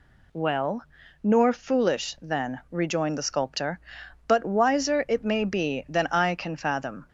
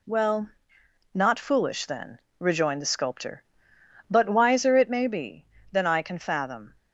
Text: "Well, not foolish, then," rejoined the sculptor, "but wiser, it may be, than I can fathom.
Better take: second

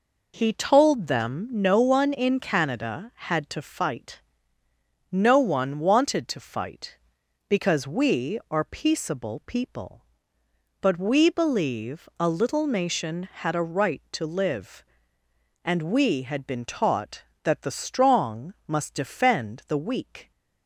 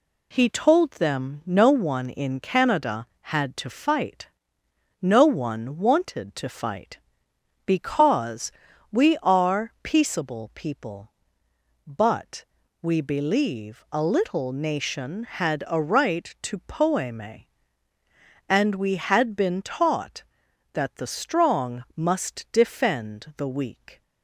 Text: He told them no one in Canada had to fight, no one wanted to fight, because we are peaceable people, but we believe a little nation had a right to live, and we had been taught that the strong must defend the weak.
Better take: first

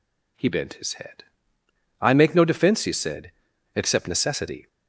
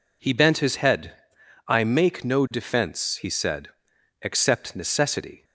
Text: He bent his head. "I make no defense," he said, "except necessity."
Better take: neither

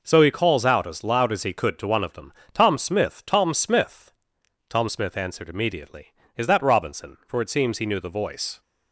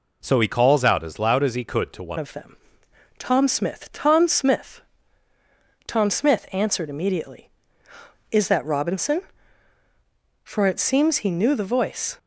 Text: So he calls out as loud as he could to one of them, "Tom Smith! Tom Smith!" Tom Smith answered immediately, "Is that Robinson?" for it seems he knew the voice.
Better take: first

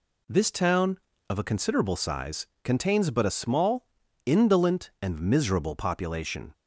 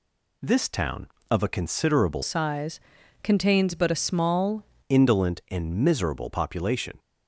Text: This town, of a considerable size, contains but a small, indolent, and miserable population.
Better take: first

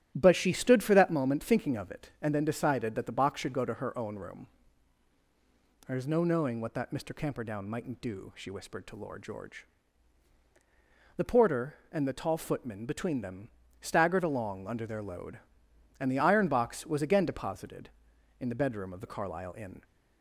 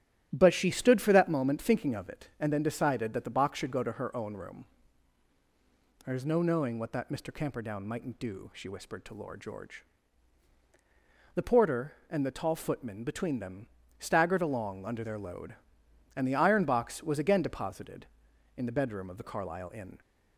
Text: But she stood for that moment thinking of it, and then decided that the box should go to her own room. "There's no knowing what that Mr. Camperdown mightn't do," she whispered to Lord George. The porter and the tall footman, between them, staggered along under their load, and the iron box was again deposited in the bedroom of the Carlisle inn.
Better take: neither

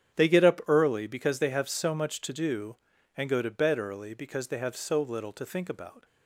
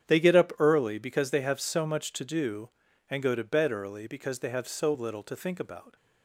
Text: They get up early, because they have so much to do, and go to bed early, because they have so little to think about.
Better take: neither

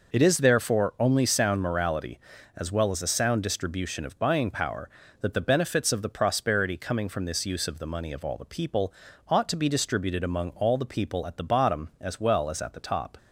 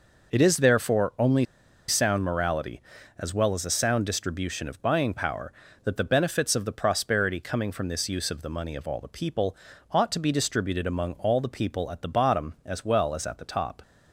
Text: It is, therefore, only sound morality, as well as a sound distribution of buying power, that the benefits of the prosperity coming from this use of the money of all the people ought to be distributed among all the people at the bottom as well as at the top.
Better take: first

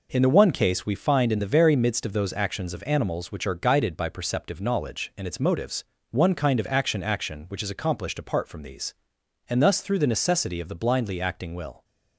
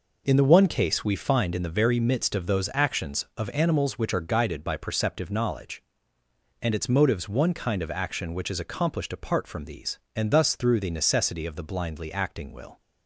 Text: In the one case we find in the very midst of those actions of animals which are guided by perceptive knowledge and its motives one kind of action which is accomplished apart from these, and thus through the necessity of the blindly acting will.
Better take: second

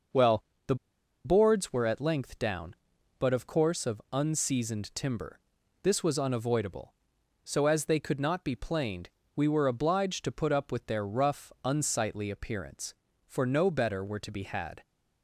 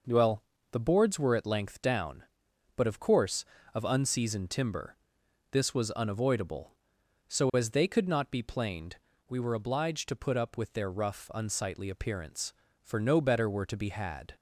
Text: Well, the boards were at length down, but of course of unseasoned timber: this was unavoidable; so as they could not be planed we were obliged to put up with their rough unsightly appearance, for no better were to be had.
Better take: second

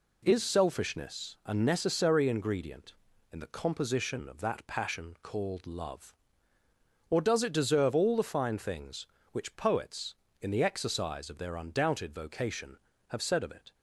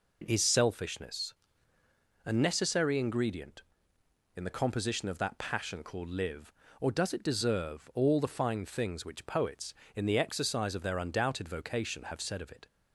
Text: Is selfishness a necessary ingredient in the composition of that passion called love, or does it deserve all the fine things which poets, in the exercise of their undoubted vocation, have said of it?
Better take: first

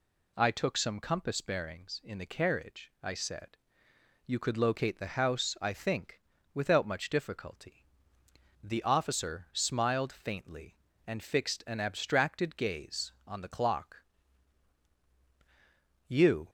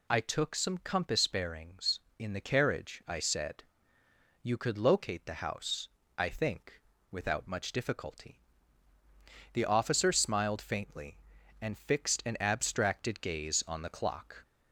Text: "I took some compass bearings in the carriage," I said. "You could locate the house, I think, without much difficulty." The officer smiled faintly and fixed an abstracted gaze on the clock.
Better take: second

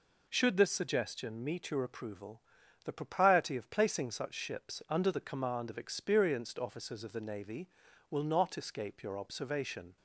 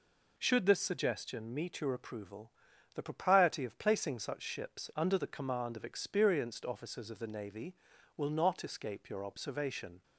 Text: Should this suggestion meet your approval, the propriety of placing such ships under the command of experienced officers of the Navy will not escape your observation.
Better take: neither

